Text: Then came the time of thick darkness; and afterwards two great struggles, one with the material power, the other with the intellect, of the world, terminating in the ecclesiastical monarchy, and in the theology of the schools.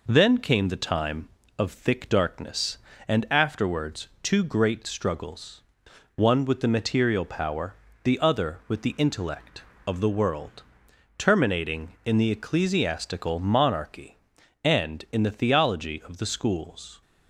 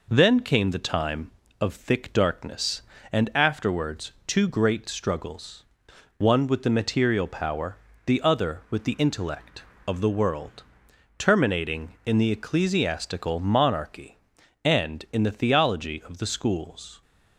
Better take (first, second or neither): neither